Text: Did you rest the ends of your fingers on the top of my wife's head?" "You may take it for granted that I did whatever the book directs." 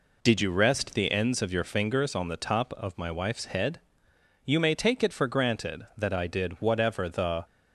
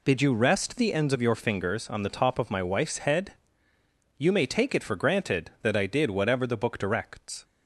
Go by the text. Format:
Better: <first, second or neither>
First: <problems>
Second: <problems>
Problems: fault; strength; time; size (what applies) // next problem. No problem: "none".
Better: second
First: stops before "book directs"; at 7.4 s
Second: none